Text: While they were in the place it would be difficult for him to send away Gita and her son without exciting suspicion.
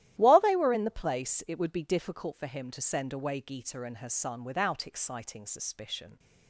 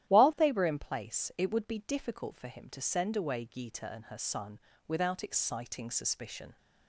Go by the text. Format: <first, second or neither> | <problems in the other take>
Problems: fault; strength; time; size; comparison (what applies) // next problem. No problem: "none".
first | starts louder than the rest; strong; until 1.1 s; 12 dB; strong in the first // skips "the"; at 0.7 s // pauses between "son" and "without"; slight; at 4.5 s; 0.28 s long